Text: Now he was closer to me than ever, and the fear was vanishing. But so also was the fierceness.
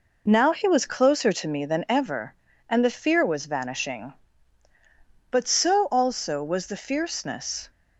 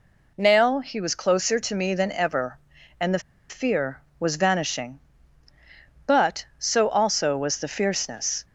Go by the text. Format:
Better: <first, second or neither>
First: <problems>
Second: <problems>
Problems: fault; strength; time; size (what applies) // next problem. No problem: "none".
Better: first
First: none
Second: pauses between "the" and "fear"; slight; at 3.1 s; 0.30 s long